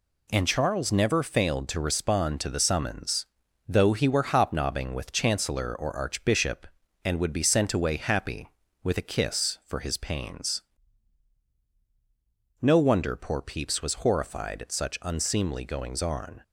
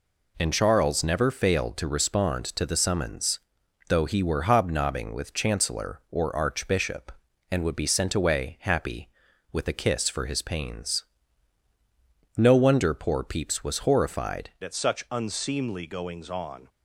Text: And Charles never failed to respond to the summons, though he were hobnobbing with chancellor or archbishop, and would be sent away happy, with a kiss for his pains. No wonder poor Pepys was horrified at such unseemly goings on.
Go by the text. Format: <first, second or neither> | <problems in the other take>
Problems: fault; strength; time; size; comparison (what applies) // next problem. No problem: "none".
first | changes voice at "at"; from 14.6 s on; 2.0 s long